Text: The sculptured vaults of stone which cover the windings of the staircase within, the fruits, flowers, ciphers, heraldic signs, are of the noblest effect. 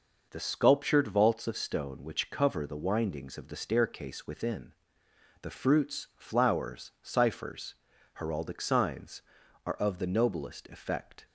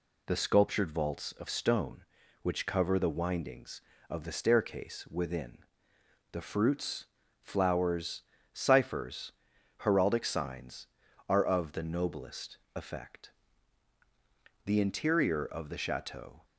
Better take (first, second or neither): first